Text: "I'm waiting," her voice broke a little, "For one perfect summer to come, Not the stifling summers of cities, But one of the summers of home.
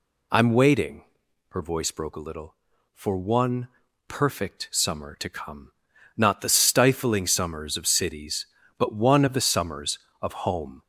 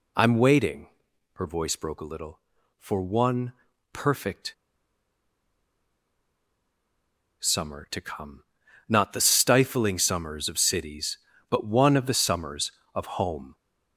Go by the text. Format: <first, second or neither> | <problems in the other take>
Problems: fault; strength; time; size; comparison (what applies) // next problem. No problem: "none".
first | pauses between "one" and "perfect"; at 3.5 s; 0.40 s long; also in the first // pauses between "perfect" and "summer"; strong; at 4.5 s; 2.8 s long